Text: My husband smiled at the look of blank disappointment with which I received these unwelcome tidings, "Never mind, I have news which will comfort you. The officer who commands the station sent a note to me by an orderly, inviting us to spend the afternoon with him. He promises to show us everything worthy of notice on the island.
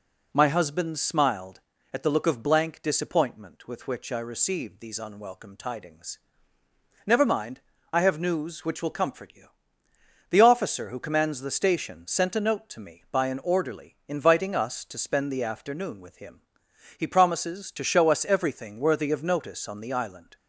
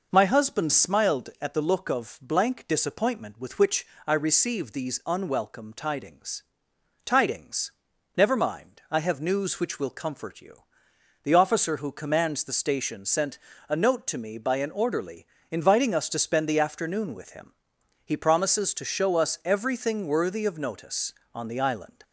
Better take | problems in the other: first | pauses between "which" and "I"; slight; at 3.8 s; 0.22 s long // says "tidings" twice; at 7.0 s // pauses between "sent" and "a"; slight; at 13.3 s; 0.30 s long

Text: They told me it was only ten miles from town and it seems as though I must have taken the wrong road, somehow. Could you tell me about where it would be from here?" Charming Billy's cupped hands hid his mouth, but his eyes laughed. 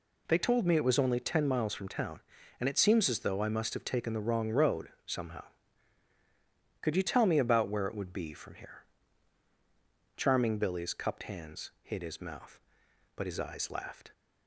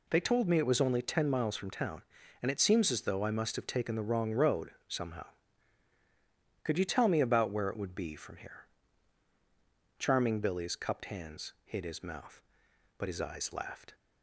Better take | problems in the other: neither | none

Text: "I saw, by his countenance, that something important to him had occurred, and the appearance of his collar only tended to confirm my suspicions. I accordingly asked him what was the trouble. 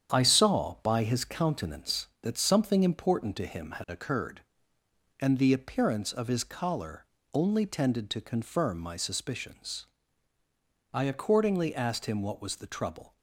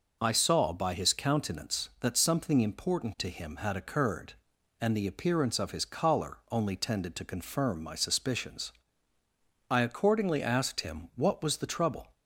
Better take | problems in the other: second | gets quieter; strong; throughout; 7.5 dB // pauses between "collar" and "only"; slight; at 7.0 s; 0.28 s long

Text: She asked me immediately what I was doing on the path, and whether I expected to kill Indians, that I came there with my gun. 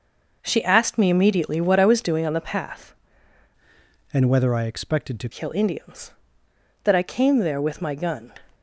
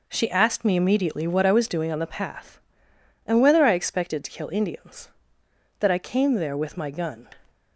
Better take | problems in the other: second | changes voice from "and" to "to"; from 4.1 to 5.2 s; 1.1 s long

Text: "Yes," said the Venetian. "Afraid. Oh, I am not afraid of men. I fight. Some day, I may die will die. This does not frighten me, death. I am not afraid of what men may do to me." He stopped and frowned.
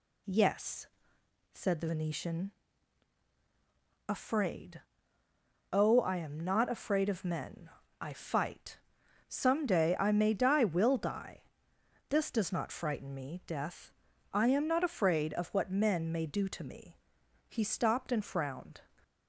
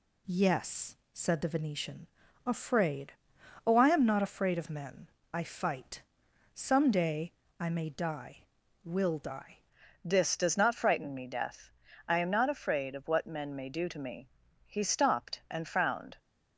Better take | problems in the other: first | changes voice at "This"; from 10.0 s on; 6.1 s long

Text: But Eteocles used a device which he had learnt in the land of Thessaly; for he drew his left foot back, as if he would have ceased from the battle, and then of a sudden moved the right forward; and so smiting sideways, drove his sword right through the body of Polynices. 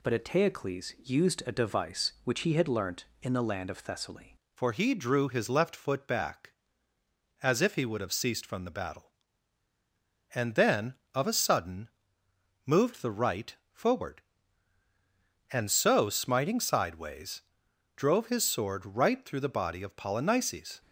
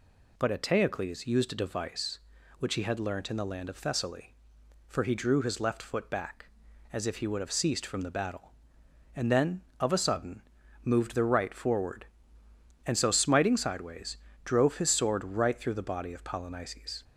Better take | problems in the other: second | changes voice at "for"; from 4.5 s on; 16.3 s long // pauses between "sudden" and "moved"; noticeable; at 11.8 s; 0.78 s long; also in the second

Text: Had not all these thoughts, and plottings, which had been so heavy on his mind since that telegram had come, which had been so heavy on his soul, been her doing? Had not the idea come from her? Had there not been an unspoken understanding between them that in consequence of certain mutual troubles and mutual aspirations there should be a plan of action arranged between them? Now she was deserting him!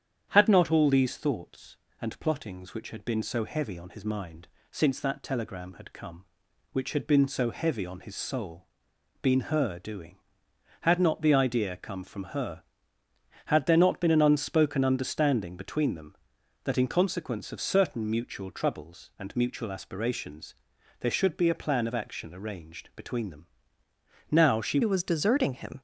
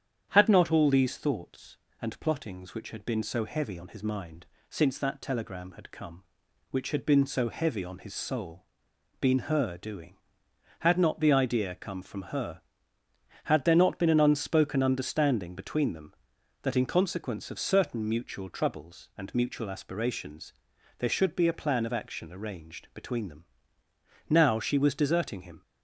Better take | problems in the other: second | starts louder than the rest; strong; until 1.3 s; 9 dB; strong in the second // pauses between "mind" and "since"; slight; at 4.4 s; 0.24 s long; slight in the second // pauses between "aspirations" and "there"; noticeable; at 20.5 s; 0.46 s long; noticeable in the second // changes voice at "was"; from 24.8 s on; 1.0 s long

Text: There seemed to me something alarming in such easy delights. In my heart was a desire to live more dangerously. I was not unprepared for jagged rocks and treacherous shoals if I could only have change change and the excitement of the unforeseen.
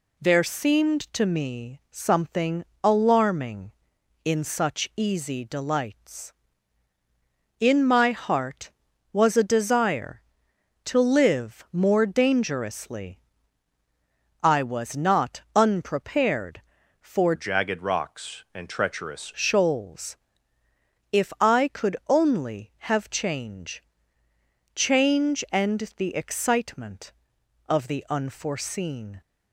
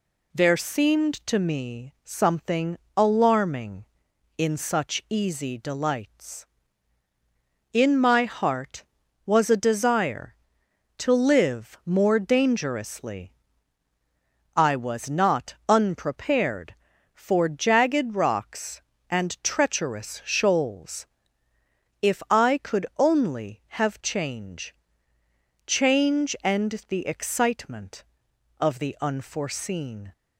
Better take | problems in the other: second | pauses between "something" and "alarming"; slight; at 2.6 s; 0.20 s long; slight in the second // changes voice from "jagged" to "treacherous"; from 17.3 to 19.3 s; 2.0 s long // pauses between "shoals" and "if"; noticeable; at 20.1 s; 0.94 s long; noticeable in the second // pauses between "change" and "change"; noticeable; at 23.8 s; 0.92 s long; noticeable in the second

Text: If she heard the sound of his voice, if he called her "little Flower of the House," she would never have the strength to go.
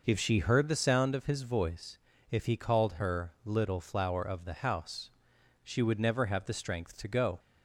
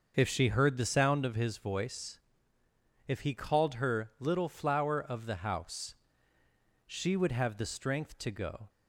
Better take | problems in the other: first | starts louder than the rest; until 1.1 s; 6.5 dB // skips "never"; at 7.3 s

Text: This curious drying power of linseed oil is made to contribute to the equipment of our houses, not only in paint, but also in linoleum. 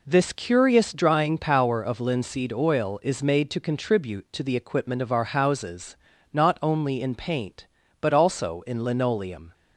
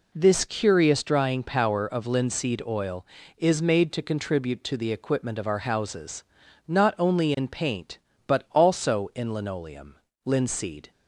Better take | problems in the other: first | goes on to say "Linseed"; noticeable; from 10.2 s on; 0.64 s long

